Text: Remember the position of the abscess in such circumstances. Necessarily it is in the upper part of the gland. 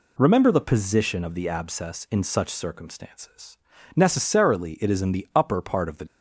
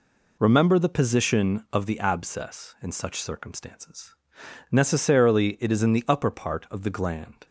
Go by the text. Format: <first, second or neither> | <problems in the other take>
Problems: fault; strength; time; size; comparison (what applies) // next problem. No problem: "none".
second | stops before "gland"; at 6.0 s